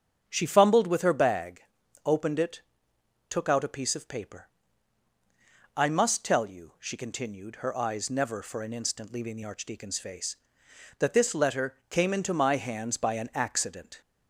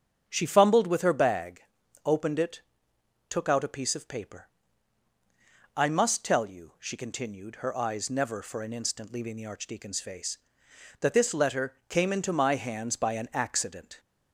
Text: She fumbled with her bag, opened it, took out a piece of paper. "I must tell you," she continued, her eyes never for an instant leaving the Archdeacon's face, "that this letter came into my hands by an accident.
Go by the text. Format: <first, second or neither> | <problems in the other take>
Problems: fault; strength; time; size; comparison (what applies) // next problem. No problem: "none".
neither | starts louder than the rest; strong; the same in both